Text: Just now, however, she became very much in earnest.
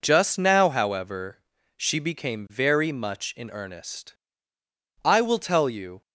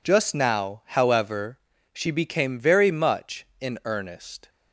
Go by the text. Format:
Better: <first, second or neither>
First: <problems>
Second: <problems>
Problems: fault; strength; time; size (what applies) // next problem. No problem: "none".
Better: second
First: goes on to say "I will tell you"; noticeable; from 5.0 s on; 0.96 s long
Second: none